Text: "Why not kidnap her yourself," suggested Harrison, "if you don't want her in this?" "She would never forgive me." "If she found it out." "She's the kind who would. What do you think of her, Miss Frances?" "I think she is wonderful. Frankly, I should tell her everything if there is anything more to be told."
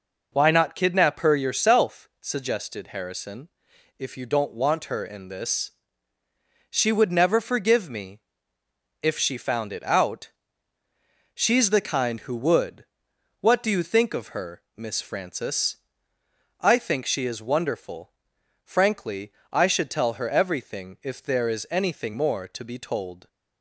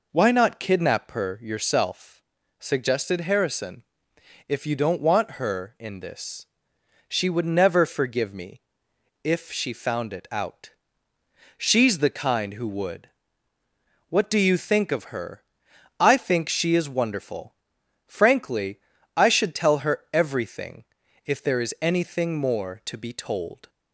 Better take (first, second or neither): first